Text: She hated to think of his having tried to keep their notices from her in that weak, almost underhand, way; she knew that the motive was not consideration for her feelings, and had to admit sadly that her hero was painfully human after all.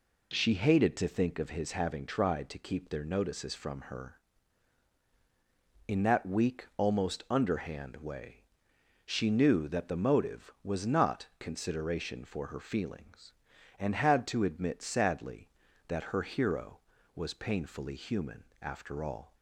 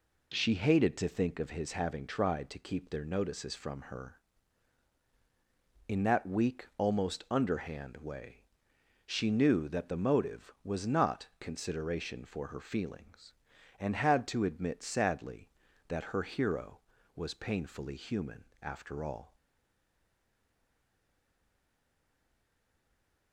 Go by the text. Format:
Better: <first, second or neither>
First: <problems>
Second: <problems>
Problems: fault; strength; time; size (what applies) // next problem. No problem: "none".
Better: first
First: pauses between "human" and "after"; slight; at 18.4 s; 0.18 s long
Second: pauses between "human" and "after"; slight; at 18.4 s; 0.18 s long // stays silent after the last word; strong; from 19.3 s on; 4.0 s long